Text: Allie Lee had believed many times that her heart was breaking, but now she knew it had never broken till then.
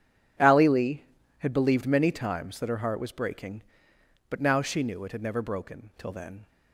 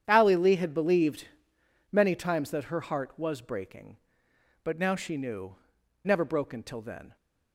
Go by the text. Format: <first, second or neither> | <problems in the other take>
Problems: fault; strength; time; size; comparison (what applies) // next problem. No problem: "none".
first | starts louder than the rest; strong; until 1.0 s; 9 dB // pauses between "believed" and "many"; noticeable; at 1.2 s; 0.62 s long // skips "it had"; at 5.8 s